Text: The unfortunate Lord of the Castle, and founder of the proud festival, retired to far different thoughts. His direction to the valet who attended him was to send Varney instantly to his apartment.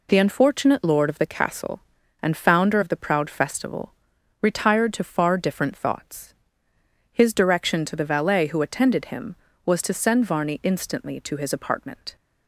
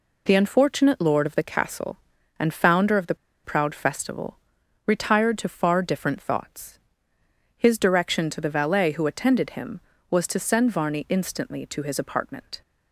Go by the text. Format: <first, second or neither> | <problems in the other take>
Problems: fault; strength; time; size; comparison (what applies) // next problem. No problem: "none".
first | pauses between "the" and "proud"; slight; at 3.1 s; 0.29 s long